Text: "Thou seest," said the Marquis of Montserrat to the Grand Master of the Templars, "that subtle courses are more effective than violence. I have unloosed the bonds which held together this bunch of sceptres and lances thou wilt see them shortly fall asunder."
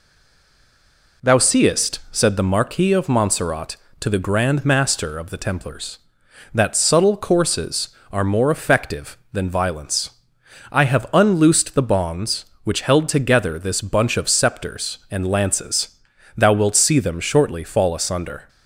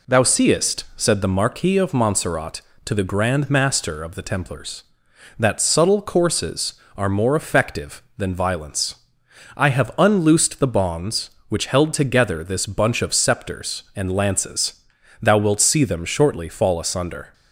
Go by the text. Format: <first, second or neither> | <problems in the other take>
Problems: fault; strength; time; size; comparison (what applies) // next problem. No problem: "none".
second | stays silent before the first word; noticeable; until 1.2 s; 1.2 s long // pauses between "lances" and "thou"; noticeable; at 15.8 s; 0.50 s long; noticeable in the second